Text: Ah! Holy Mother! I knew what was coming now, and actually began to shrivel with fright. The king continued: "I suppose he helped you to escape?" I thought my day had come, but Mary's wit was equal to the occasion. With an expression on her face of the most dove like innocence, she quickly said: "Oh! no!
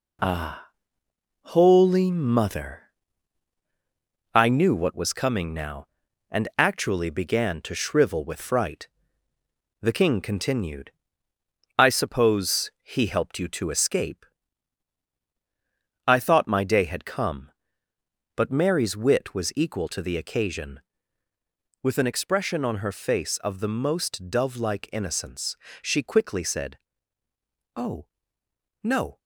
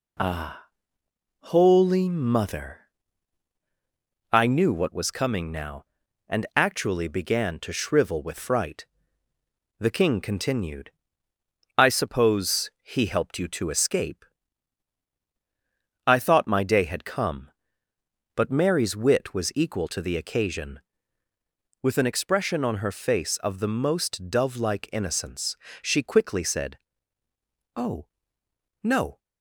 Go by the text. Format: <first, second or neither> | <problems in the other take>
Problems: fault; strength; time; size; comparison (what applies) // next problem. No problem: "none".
second | gets quieter; throughout; 6 dB